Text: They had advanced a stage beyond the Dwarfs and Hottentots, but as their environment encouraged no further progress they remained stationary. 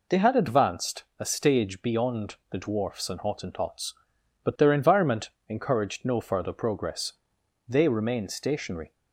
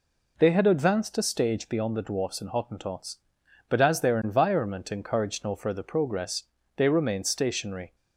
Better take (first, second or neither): second